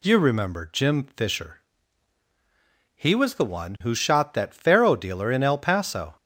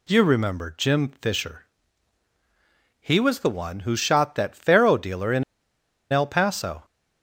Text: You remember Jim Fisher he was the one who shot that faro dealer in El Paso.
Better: first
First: pauses between "Fisher" and "he"; strong; at 1.6 s; 1.3 s long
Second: pauses between "Fisher" and "he"; strong; at 1.6 s; 1.3 s long // pauses between "in" and "El"; noticeable; at 5.4 s; 0.69 s long

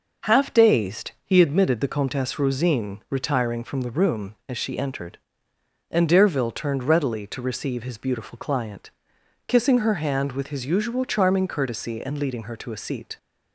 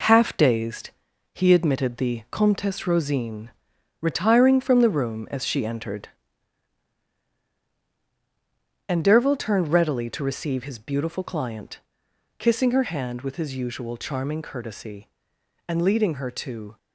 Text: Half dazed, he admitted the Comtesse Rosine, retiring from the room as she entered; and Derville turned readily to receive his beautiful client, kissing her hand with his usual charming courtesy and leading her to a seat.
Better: first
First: none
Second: stops before "a seat"; at 16.7 s

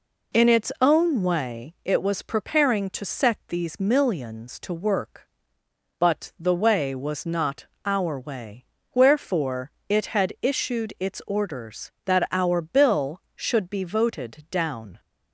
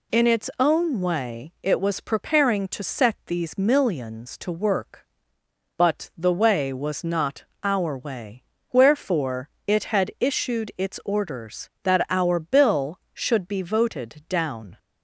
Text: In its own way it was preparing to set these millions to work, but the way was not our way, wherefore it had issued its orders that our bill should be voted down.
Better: second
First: starts louder than the rest; until 1.5 s; 3.5 dB // pauses between "not" and "our"; slight; at 7.6 s; 0.18 s long // pauses between "wherefore" and "it"; slight; at 9.7 s; 0.18 s long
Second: pauses between "not" and "our"; slight; at 7.4 s; 0.18 s long // pauses between "wherefore" and "it"; slight; at 9.4 s; 0.18 s long

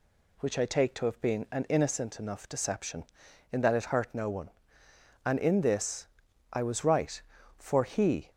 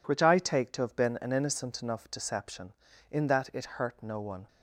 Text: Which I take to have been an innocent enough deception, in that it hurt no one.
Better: second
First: goes on to say "And in this I was right for he"; strong; from 5.2 s on; 3.0 s long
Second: none

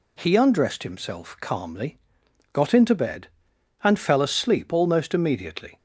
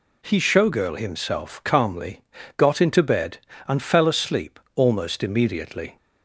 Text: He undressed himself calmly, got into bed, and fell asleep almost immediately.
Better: first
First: none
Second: says "showgirl" for "undressed"; at 0.3 s // pauses between "asleep" and "almost"; slight; at 4.5 s; 0.16 s long

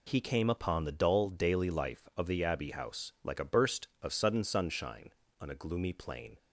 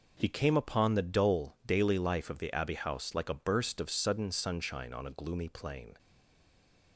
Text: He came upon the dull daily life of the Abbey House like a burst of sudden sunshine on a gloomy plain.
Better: first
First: none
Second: stays silent after the last word; from 5.9 s on; 1.0 s long

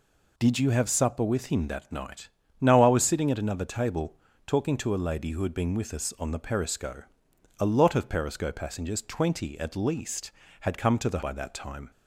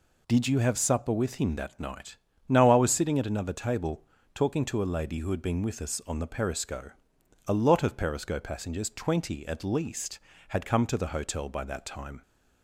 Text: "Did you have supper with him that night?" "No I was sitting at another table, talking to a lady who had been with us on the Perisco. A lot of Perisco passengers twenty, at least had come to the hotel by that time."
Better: second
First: skips "hotel"; at 11.2 s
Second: none

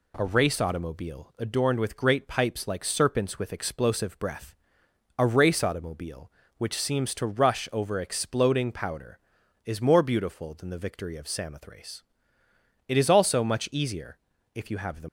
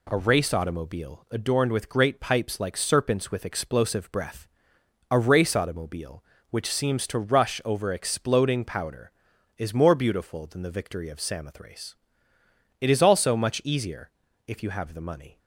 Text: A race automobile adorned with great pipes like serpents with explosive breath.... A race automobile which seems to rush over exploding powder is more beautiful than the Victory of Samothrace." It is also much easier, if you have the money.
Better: second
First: stops before "money"; at 15.0 s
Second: none

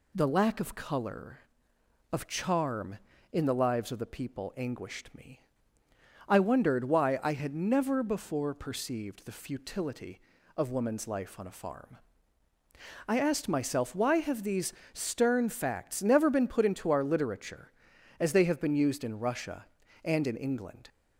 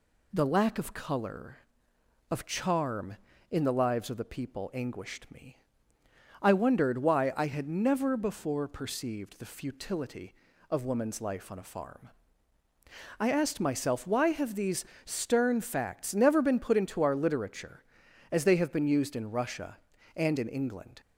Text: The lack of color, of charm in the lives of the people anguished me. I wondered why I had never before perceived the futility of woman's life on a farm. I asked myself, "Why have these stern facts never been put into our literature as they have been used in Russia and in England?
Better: neither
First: pauses between "these" and "stern"; slight; at 14.7 s; 0.22 s long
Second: pauses between "these" and "stern"; slight; at 14.8 s; 0.22 s long

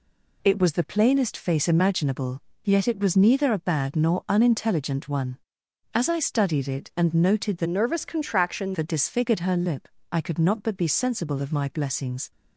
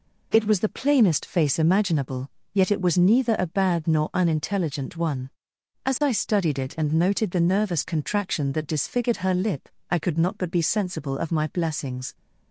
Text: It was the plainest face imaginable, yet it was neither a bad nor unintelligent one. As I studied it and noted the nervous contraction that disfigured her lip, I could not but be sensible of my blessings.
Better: second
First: changes voice from "nervous" to "contraction"; from 7.6 to 8.7 s; 1.1 s long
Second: none

